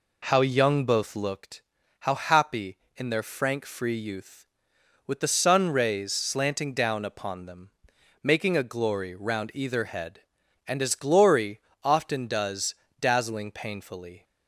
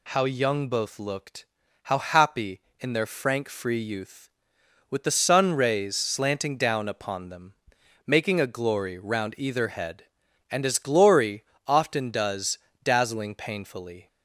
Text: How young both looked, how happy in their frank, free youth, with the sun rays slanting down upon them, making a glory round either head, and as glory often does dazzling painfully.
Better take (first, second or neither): second